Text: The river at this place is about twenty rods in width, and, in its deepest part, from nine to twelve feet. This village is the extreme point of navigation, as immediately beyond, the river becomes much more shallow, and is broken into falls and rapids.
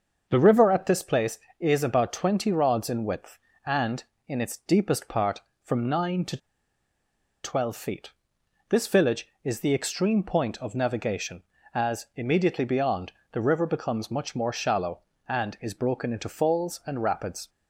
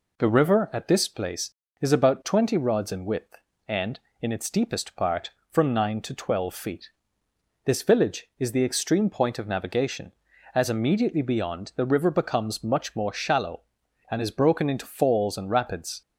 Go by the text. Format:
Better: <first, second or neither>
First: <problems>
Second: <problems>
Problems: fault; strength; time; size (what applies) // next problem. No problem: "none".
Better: second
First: starts louder than the rest; until 1.3 s; 6.5 dB // pauses between "to" and "twelve"; at 6.3 s; 1.0 s long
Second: none